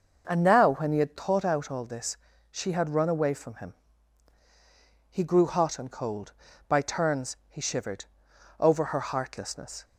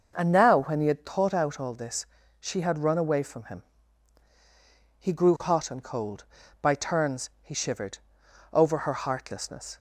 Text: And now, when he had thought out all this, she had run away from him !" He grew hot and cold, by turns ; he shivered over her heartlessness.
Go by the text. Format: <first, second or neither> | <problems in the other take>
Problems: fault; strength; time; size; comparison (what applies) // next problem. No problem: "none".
neither | starts louder than the rest; the same in both // pauses between "shivered" and "over"; noticeable; the same in both